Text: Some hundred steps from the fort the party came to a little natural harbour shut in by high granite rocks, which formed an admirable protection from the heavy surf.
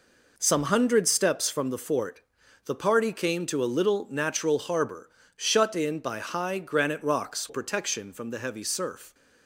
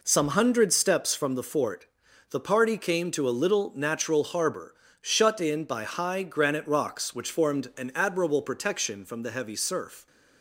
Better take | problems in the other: second | pauses between "fort" and "the"; noticeable; at 2.2 s; 0.46 s long; noticeable in the second // pauses between "harbour" and "shut"; slight; at 5.0 s; 0.26 s long; slight in the second // skips "which formed an admirable"; at 7.4 s

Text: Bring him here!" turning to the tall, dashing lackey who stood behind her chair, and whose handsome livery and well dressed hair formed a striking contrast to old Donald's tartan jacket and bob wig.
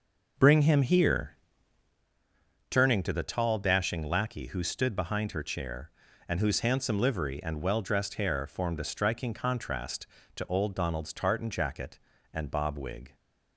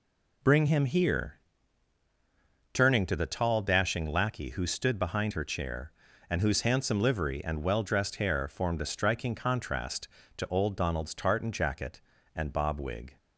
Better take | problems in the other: second | starts louder than the rest; noticeable; until 2.1 s; 5.5 dB

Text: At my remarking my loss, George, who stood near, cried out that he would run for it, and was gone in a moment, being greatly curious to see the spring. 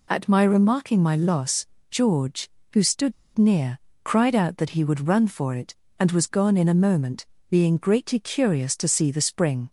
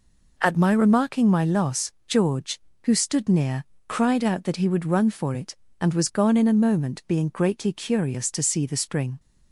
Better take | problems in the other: second | pauses between "stood" and "near"; slight; at 3.1 s; 0.23 s long

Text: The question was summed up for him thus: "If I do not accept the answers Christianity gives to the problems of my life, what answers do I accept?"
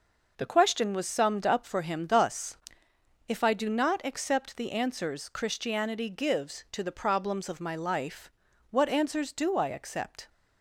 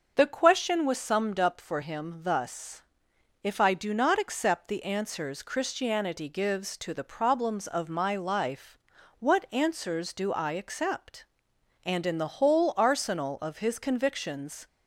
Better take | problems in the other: first | starts louder than the rest; until 1.1 s; 6.5 dB // goes on to say "And in the whole arsenal of his convictions"; strong; from 11.8 s on; 2.8 s long

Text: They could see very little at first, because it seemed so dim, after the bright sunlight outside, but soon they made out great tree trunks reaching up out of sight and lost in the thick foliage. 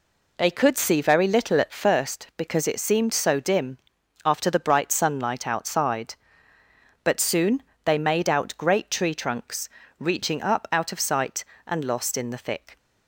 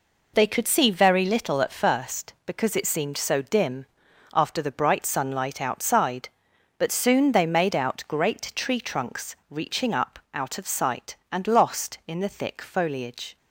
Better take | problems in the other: second | pauses between "soon" and "they"; slight; at 7.6 s; 0.22 s long // pauses between "trunks" and "reaching"; slight; at 9.6 s; 0.28 s long // stops before "foliage"; at 12.7 s

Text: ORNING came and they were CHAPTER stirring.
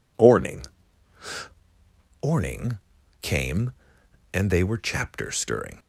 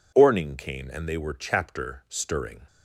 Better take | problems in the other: second | says "ORNING" twice; at 2.2 s

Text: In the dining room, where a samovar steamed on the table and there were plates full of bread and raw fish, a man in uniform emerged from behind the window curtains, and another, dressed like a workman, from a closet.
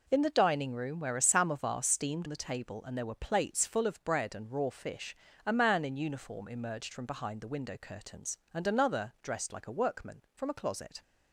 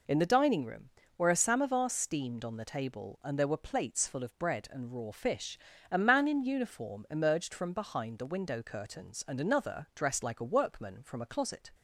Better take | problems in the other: second | skips "on"; at 2.2 s

